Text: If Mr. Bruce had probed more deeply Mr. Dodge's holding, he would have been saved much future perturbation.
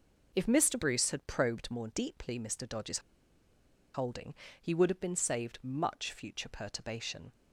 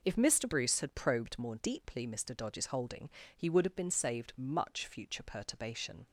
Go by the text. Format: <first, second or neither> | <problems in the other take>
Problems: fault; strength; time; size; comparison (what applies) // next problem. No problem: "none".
second | pauses between "Dodge's" and "holding"; noticeable; at 2.9 s; 0.94 s long